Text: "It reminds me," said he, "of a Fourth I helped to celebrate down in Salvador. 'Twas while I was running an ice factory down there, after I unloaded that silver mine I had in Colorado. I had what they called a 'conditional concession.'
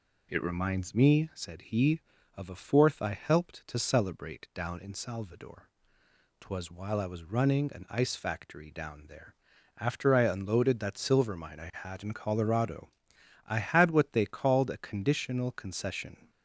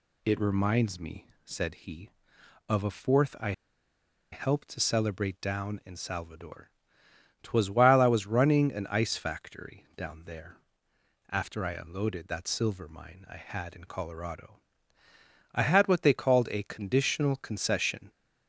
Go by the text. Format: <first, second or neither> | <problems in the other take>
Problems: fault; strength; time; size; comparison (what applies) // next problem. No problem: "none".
first | pauses between "I" and "helped"; noticeable; at 3.5 s; 0.79 s long